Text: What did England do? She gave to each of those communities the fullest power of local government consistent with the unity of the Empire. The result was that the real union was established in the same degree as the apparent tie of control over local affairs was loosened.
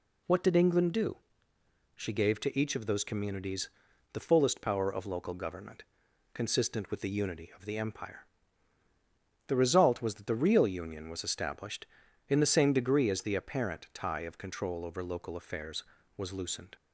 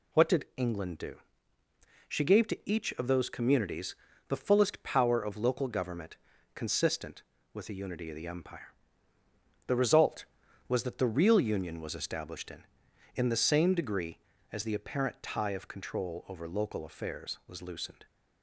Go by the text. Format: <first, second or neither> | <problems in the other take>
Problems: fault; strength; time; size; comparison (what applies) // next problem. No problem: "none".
first | pauses between "communities" and "the"; slight; at 3.9 s; 0.34 s long; also in the first // pauses between "government" and "consistent"; at 6.1 s; 0.40 s long; noticeable in the first // says "in" twice; at 13.1 s